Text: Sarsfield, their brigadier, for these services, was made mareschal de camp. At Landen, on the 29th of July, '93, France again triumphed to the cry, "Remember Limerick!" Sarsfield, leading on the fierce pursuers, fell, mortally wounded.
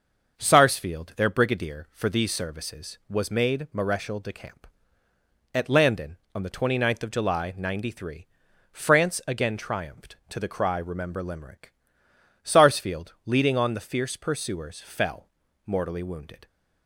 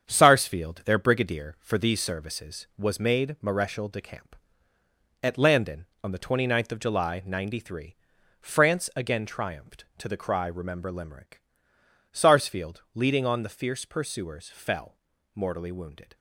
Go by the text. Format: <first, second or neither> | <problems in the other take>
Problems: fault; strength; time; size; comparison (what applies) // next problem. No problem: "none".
first | gets quieter; throughout; 7 dB // starts louder than the rest; strong; until 1.0 s; 7.5 dB; also in the first